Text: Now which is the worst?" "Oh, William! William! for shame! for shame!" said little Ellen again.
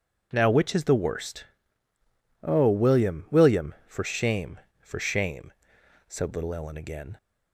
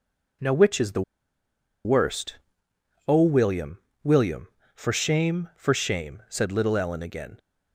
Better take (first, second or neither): first